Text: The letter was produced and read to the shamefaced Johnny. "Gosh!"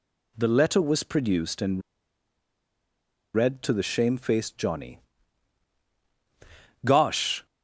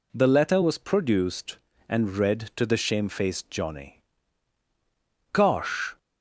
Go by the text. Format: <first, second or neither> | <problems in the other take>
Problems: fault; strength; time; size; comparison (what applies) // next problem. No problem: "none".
second | pauses between "and" and "read"; strong; at 1.8 s; 1.5 s long